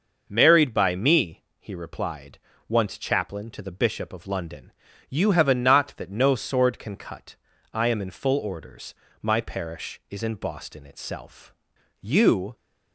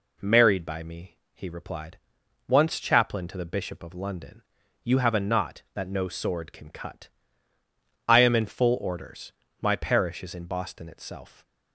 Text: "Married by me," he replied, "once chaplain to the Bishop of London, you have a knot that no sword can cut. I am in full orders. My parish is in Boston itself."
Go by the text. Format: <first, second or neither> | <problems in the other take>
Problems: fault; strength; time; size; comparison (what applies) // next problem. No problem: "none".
second | goes on to say "You"; from 11.9 s on; 0.56 s long